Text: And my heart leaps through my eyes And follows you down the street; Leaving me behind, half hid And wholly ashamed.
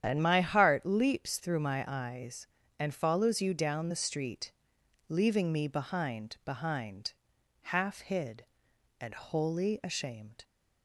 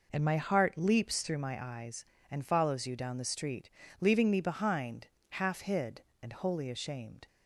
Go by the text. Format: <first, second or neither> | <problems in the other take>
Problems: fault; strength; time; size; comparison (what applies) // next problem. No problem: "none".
second | starts louder than the rest; strong; until 1.0 s; 9 dB // says "behind" twice; at 6.4 s